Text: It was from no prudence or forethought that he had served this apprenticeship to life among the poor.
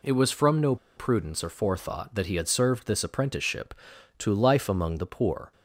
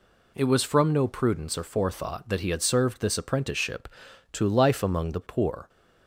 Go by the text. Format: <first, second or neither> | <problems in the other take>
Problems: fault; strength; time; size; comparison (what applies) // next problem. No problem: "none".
second | pauses between "no" and "prudence"; slight; at 0.7 s; 0.21 s long